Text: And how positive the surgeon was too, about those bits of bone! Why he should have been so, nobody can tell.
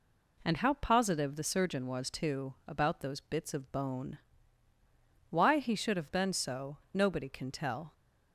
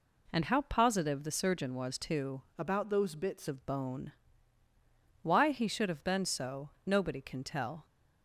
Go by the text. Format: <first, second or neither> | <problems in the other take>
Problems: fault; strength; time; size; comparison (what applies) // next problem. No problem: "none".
first | changes voice from "about" to "bits"; from 2.5 to 3.4 s; 0.9 s long